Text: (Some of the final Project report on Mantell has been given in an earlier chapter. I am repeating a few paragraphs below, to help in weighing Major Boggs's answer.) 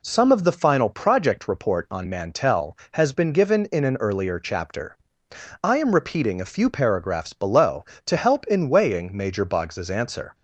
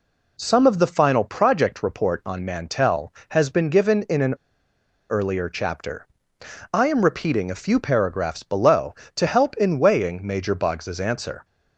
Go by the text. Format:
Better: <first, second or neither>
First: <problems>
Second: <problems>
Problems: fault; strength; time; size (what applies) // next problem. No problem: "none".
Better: first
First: none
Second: pauses between "an" and "earlier"; noticeable; at 4.3 s; 0.74 s long